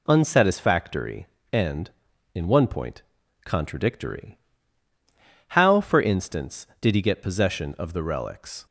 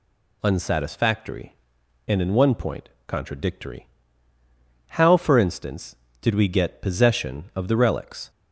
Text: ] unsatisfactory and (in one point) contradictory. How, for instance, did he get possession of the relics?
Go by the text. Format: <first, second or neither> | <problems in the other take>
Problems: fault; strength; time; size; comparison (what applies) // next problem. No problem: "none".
first | says "we" for "he"; at 6.3 s